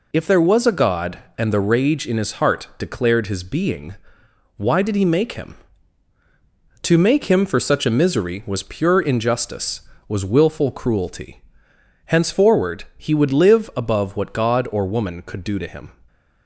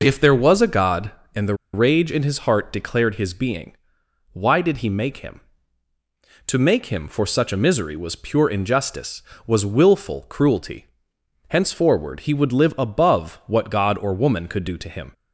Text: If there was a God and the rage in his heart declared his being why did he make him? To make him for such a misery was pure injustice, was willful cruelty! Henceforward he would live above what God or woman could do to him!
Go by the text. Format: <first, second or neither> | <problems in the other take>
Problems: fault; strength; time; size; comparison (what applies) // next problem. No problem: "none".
first | pauses between "the" and "rage"; slight; at 1.5 s; 0.19 s long // pauses between "being" and "why"; noticeable; at 3.7 s; 0.56 s long; noticeable in the first